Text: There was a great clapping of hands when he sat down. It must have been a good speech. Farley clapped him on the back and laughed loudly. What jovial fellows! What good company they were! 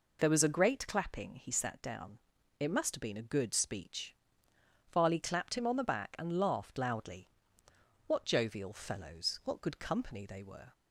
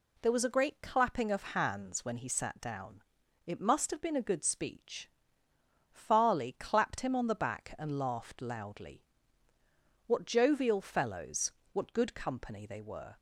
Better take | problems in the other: second | skips "of hands when"; at 1.3 s

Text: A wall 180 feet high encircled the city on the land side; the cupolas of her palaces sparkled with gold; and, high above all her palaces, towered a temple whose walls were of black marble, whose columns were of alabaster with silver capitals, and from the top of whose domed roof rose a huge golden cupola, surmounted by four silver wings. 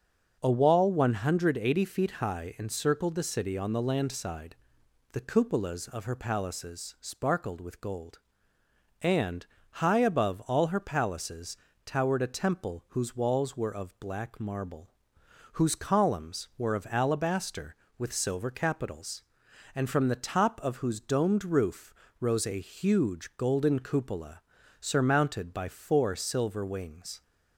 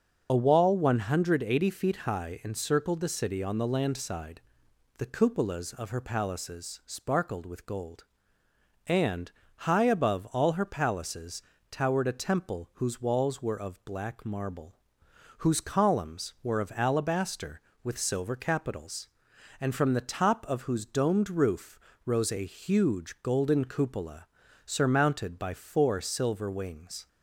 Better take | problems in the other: first | loses the start of "A"; at 0.2 s; 45 ms // starts louder than the rest; until 1.3 s; 6 dB; also in the first // pauses between "roof" and "rose"; slight; at 21.7 s; 0.28 s long; slight in the first

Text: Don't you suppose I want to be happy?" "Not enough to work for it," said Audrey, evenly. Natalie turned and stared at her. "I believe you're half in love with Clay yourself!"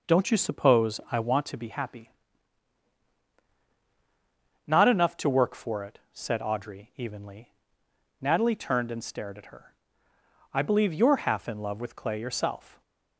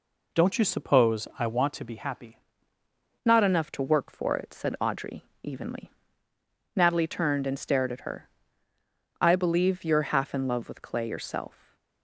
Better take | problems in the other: first | changes voice at "Not"; from 3.2 s on; 8.5 s long // stays silent after the last word; slight; from 11.4 s on; 0.6 s long

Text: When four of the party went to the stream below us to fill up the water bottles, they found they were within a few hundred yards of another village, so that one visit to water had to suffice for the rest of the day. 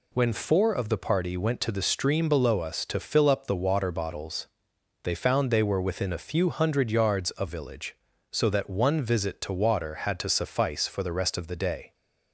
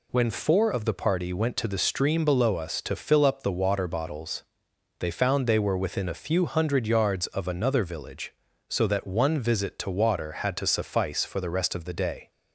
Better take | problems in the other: second | skips "another"; at 7.4 s

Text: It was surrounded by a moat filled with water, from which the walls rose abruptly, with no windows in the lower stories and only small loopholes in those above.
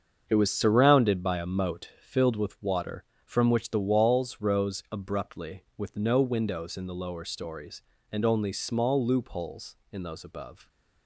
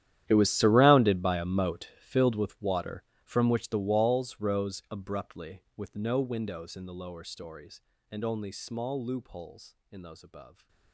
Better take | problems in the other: first | gets quieter; strong; throughout; 18.5 dB // starts louder than the rest; strong; until 1.2 s; 11.5 dB; also in the first

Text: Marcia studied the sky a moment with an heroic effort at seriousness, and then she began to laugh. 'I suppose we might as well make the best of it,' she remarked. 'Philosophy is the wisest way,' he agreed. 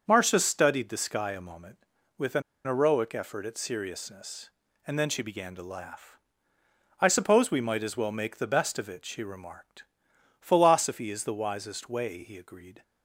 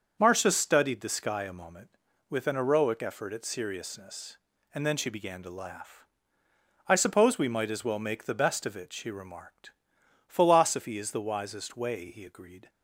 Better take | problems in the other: second | starts louder than the rest; until 1.0 s; 6.5 dB; also in the second // pauses between "an" and "heroic"; slight; at 2.4 s; 0.23 s long

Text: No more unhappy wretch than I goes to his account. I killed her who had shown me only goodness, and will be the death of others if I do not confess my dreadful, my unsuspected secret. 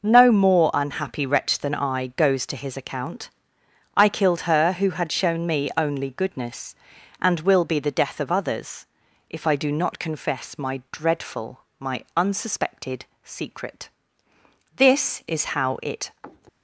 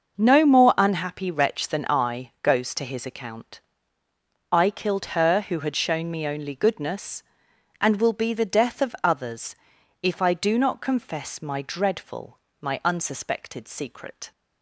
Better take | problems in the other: second | pauses between "others" and "if"; at 8.8 s; 0.42 s long; also in the second // pauses between "unsuspected" and "secret"; slight; at 13.0 s; 0.20 s long // goes on to say "This is how it"; from 14.7 s on; 1.3 s long

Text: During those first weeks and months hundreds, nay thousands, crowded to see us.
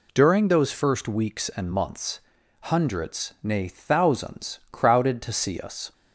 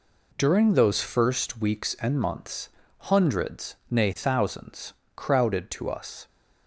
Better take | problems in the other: first | pauses between "months" and "hundreds"; at 2.6 s; 0.42 s long; also in the first // skips "see"; at 5.8 s

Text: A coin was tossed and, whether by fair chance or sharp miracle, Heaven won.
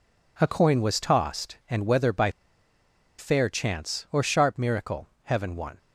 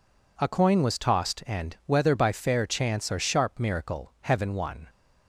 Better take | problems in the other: second | pauses between "by" and "fair"; noticeable; at 2.2 s; 0.89 s long

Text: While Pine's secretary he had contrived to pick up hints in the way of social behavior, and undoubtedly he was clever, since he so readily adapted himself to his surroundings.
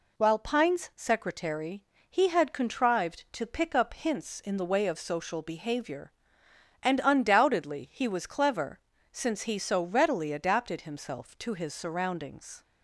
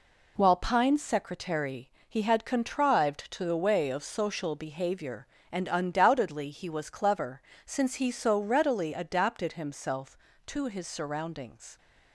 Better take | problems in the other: first | pauses between "secretary" and "he"; slight; at 1.8 s; 0.18 s long; slight in the first // skips "pick up hints in"; at 3.4 s

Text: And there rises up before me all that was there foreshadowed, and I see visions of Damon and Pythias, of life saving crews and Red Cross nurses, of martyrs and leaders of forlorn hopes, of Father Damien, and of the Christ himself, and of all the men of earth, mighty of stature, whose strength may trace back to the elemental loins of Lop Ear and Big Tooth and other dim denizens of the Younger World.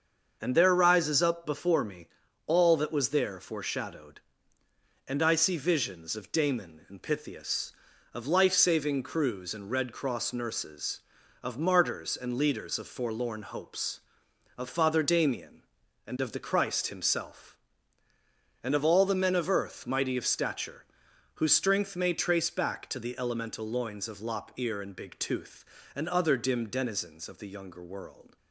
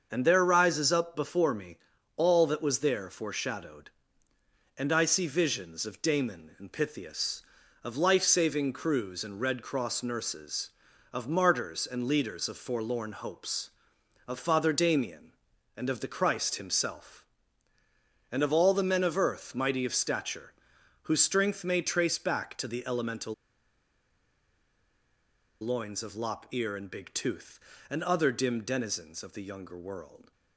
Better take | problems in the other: first | starts louder than the rest; until 1.1 s; 6.5 dB; also in the first // pauses between "me" and "all"; at 1.7 s; 0.40 s long; also in the first // pauses between "elemental" and "loins"; strong; at 23.3 s; 2.2 s long

